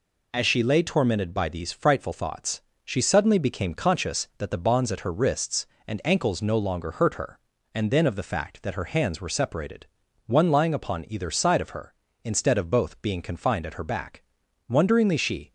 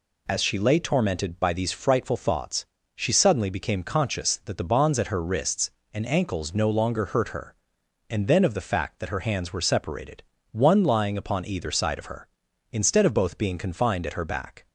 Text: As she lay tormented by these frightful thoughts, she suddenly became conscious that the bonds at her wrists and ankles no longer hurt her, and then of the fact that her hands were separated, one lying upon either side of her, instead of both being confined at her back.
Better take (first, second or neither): second